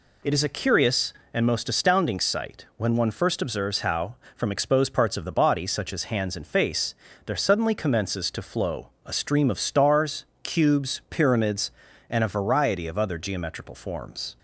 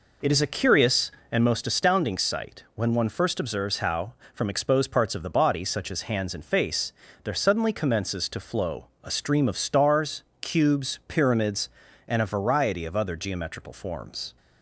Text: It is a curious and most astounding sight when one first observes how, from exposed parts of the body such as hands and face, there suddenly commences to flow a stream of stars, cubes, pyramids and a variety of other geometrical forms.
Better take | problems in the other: first | starts louder than the rest; noticeable; until 1.7 s; 4.5 dB // pauses between "flow" and "a"; slight; at 8.8 s; 0.18 s long; slight in the first

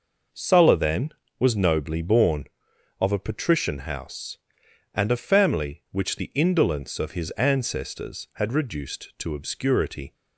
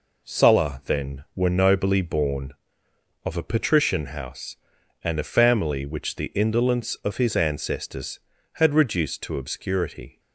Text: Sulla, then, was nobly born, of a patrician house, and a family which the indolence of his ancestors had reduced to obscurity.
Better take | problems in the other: first | says "were" for "was"; at 1.3 s

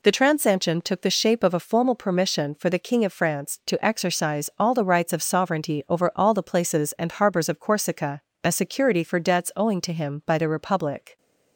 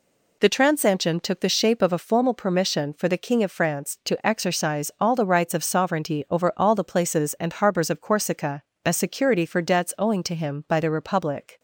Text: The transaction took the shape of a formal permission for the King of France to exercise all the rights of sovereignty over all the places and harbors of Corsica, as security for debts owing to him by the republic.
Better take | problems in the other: neither | none

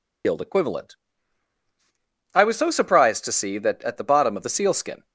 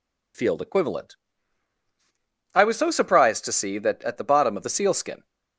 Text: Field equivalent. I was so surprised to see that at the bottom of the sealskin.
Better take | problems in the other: second | loses the start of "Field"; at 0.2 s; 105 ms

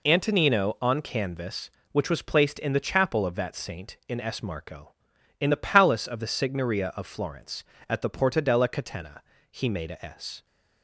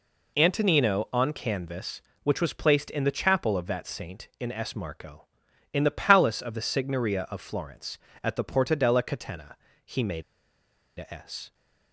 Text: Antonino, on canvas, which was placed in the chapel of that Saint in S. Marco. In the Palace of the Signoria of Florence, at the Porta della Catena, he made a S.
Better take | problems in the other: first | pauses between "made" and "a"; noticeable; at 10.2 s; 0.76 s long

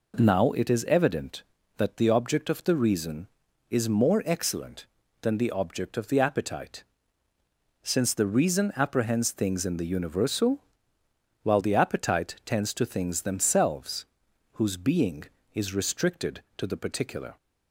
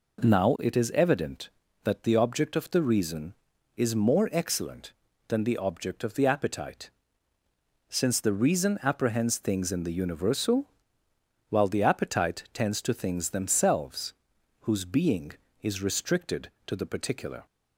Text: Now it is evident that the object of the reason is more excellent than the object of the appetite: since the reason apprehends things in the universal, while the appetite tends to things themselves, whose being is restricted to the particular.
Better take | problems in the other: neither | none

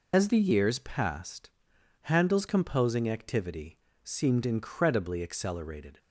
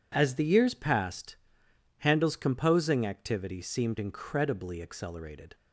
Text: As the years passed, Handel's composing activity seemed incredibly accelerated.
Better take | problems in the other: second | loses the start of "As"; at 0.1 s; 55 ms // pauses between "activity" and "seemed"; slight; at 3.7 s; 0.28 s long

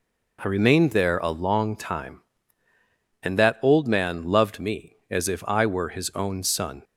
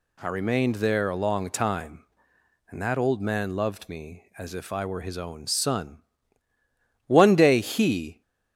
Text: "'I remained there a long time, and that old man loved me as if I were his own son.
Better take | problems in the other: first | goes on to say "One day he"; noticeable; from 7.0 s on; 1.1 s long

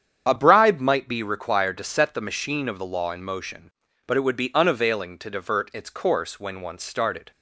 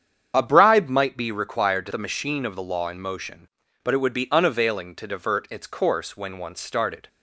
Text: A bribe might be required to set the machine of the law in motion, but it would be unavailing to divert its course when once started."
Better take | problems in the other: first | starts louder than the rest; strong; until 1.3 s; 8 dB; strong in the first // skips "set"; at 1.9 s

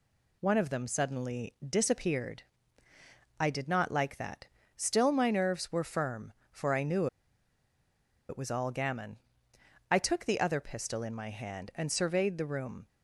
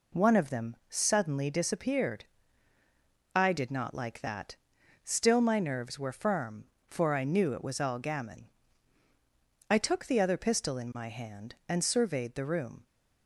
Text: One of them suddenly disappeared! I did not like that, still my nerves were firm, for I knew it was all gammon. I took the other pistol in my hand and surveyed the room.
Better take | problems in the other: second | pauses between "knew" and "it"; at 7.0 s; 1.2 s long

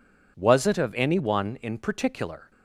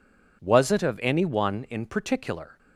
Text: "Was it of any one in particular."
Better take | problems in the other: neither | none

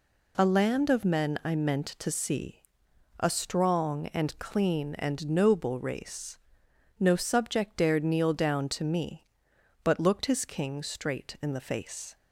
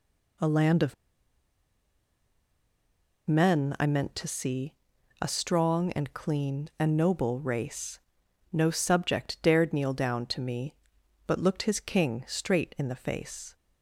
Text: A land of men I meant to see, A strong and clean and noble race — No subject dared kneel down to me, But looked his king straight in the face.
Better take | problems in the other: first | pauses between "of" and "men"; strong; at 0.9 s; 2.3 s long

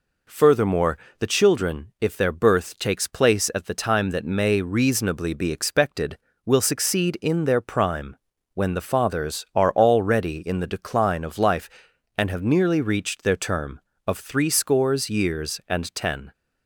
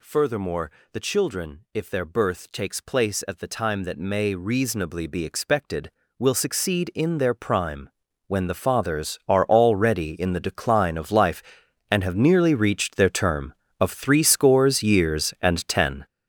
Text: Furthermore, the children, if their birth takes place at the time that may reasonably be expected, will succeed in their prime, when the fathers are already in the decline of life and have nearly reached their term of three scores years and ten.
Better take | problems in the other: first | gets louder; strong; throughout; 9.5 dB

